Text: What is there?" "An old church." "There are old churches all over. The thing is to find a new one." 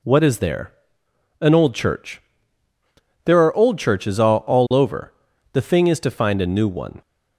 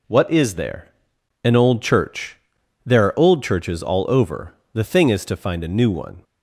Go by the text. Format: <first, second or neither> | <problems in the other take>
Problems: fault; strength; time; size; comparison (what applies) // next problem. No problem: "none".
second | says "all" twice; at 4.4 s